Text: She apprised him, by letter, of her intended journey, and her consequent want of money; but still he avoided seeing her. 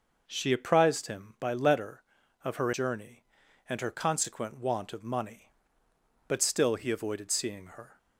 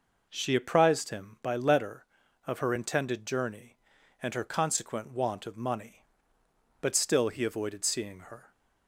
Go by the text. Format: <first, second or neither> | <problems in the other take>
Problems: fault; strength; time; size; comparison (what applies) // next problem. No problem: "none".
second | skips "intended"; at 2.7 s